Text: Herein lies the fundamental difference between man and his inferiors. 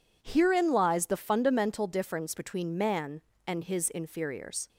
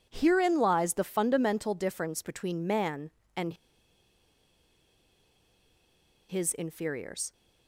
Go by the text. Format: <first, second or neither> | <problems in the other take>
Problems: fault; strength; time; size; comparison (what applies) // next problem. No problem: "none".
first | pauses between "and" and "his"; strong; at 3.5 s; 2.7 s long